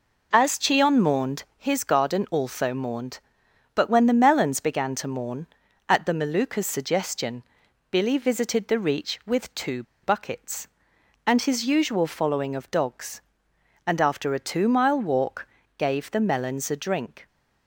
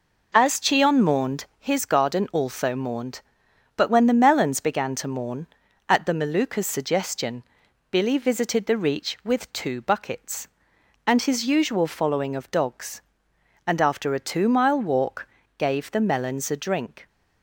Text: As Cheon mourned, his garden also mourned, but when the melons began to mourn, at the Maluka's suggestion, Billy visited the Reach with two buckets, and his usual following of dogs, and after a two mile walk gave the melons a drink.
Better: second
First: pauses between "two" and "buckets"; slight; at 9.8 s; 0.20 s long // pauses between "walk" and "gave"; slight; at 15.4 s; 0.30 s long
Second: pauses between "walk" and "gave"; slight; at 15.2 s; 0.30 s long

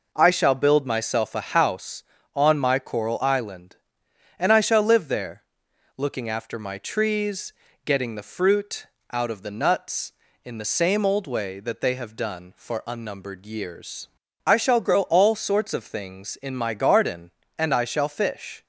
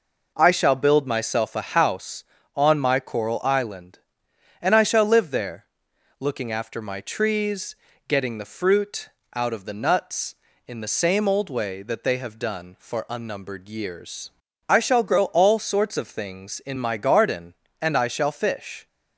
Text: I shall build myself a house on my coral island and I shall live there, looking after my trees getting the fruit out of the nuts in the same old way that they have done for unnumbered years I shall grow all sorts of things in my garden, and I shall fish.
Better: neither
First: pauses between "trees" and "getting"; slight; at 7.5 s; 0.34 s long // pauses between "fruit" and "out"; slight; at 8.8 s; 0.26 s long // pauses between "years" and "I"; at 14.0 s; 0.38 s long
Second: pauses between "trees" and "getting"; slight; at 7.7 s; 0.34 s long // pauses between "fruit" and "out"; slight; at 9.0 s; 0.26 s long // pauses between "years" and "I"; at 14.3 s; 0.38 s long

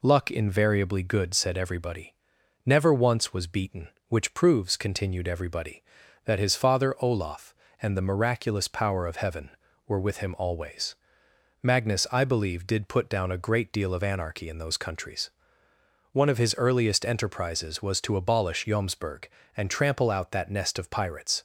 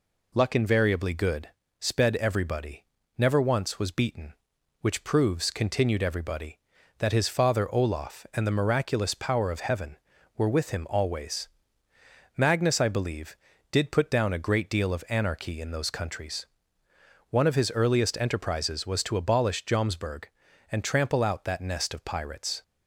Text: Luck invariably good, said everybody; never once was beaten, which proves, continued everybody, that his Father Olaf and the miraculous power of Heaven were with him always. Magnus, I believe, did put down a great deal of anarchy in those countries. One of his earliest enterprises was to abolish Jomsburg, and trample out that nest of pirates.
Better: first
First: none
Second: says "sped" for "said"; at 1.7 s

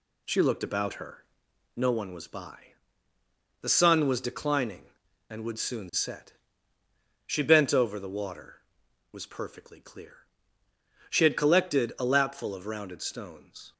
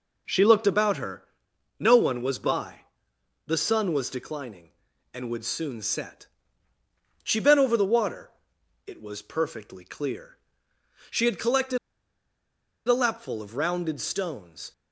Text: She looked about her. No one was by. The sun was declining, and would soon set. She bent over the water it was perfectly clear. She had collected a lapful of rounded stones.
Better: first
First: pauses between "water" and "it"; noticeable; at 8.6 s; 0.46 s long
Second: pauses between "water" and "it"; noticeable; at 8.3 s; 0.56 s long // pauses between "collected" and "a"; at 11.7 s; 1.1 s long

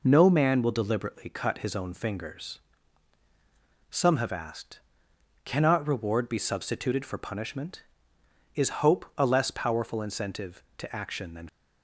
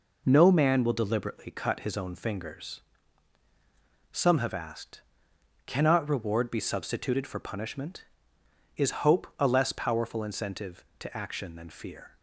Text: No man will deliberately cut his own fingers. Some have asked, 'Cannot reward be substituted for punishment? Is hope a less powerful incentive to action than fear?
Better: second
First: stops before "fear"; at 11.4 s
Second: none

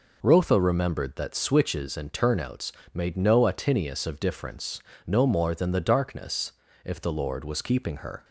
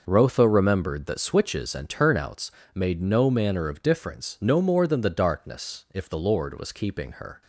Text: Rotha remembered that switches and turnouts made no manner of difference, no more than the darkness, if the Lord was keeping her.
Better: second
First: pauses between "turnouts" and "made"; slight; at 2.7 s; 0.20 s long // says "atinius" for "manner"; at 3.4 s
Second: pauses between "turnouts" and "made"; slight; at 2.5 s; 0.24 s long

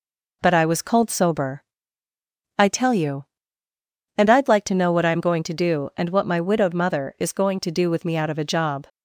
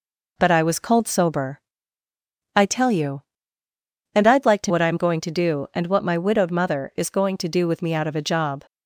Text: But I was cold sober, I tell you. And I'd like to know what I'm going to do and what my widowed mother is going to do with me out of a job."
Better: first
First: none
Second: skips "know"; at 4.7 s

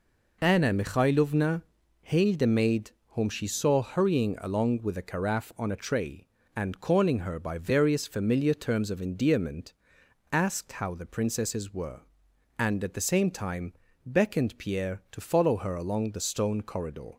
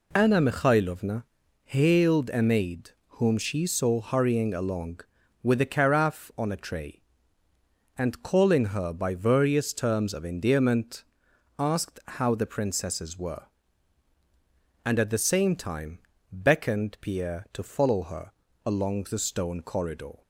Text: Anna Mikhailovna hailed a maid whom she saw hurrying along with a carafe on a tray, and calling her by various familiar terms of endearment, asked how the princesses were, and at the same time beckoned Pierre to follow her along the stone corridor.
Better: first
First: pauses between "Mikhailovna" and "hailed"; at 1.6 s; 0.40 s long // pauses between "maid" and "whom"; slight; at 2.9 s; 0.22 s long // pauses between "time" and "beckoned"; slight; at 13.7 s; 0.32 s long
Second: pauses between "Mikhailovna" and "hailed"; at 1.2 s; 0.40 s long // pauses between "maid" and "whom"; slight; at 2.8 s; 0.22 s long // skips "familiar"; at 9.7 s // pauses between "time" and "beckoned"; slight; at 15.9 s; 0.32 s long // pauses between "her" and "along"; slight; at 18.3 s; 0.34 s long

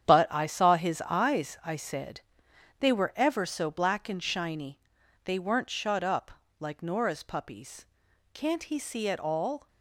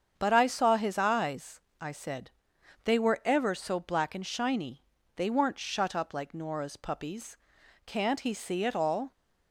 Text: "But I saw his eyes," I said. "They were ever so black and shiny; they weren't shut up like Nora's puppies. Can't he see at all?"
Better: second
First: gets quieter; strong; throughout; 10 dB // starts louder than the rest; strong; until 1.1 s; 9.5 dB // pauses between "up" and "like"; slight; at 6.3 s; 0.28 s long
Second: starts louder than the rest; strong; until 1.1 s; 7.5 dB

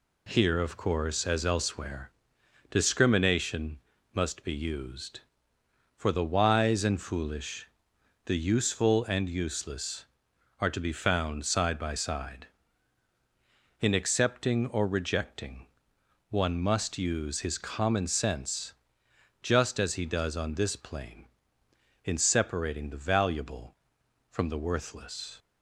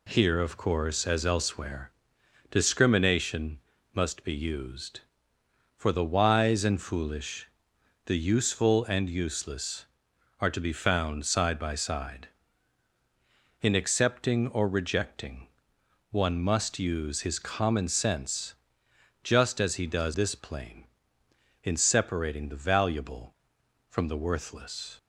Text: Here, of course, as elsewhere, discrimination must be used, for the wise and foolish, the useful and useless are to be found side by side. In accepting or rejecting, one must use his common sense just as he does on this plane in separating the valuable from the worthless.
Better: first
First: pauses between "discrimination" and "must"; slight; at 3.7 s; 0.34 s long // pauses between "sense" and "just"; noticeable; at 18.7 s; 0.70 s long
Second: pauses between "discrimination" and "must"; slight; at 3.5 s; 0.34 s long // pauses between "sense" and "just"; noticeable; at 18.5 s; 0.70 s long // skips "on"; at 20.1 s

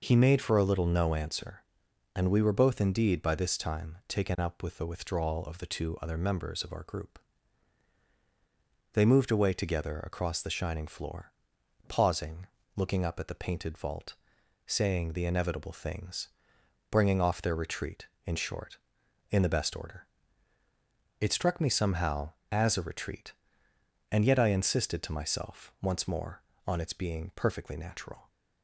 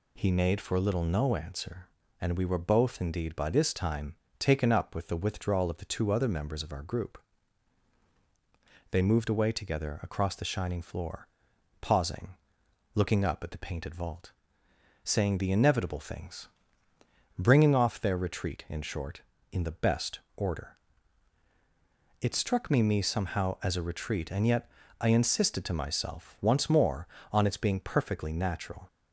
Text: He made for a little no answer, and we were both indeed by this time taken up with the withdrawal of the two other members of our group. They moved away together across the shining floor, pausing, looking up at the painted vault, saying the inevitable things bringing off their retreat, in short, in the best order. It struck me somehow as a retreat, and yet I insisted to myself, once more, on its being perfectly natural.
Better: first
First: pauses between "things" and "bringing"; noticeable; at 16.2 s; 0.64 s long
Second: pauses between "time" and "taken"; slight; at 4.1 s; 0.24 s long // pauses between "things" and "bringing"; noticeable; at 16.4 s; 0.90 s long // pauses between "best" and "order"; slight; at 20.2 s; 0.16 s long // says "me" twice; at 22.8 s // pauses between "yet" and "I"; slight; at 24.7 s; 0.30 s long

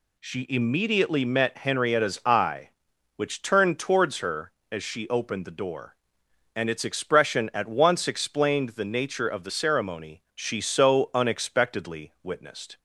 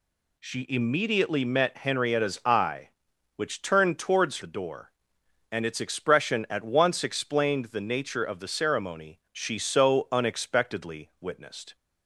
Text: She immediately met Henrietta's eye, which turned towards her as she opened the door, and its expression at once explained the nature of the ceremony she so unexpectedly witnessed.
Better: first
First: none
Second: skips "her as she opened"; at 4.4 s

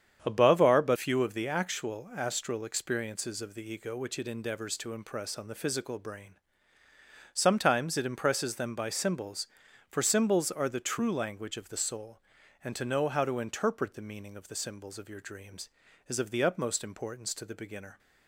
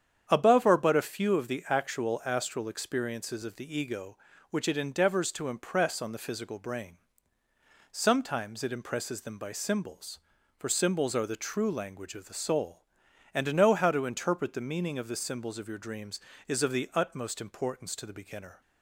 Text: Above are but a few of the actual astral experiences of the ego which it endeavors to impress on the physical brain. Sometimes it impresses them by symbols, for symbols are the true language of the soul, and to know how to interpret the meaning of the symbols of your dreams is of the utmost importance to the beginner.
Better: second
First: starts louder than the rest; strong; until 1.2 s; 8.5 dB // skips "a"; at 0.9 s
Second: starts louder than the rest; strong; until 1.2 s; 8.5 dB

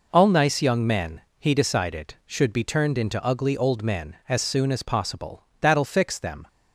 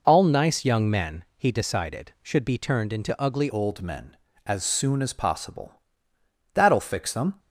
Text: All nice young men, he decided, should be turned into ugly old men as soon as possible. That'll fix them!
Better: first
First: none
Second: changes voice at "old"; from 3.4 s on; 3.9 s long

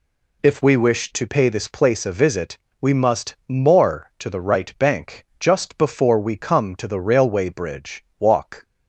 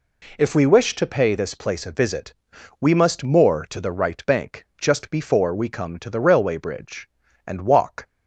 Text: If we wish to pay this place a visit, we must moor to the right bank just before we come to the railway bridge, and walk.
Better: second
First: skips "and"; at 8.1 s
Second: none

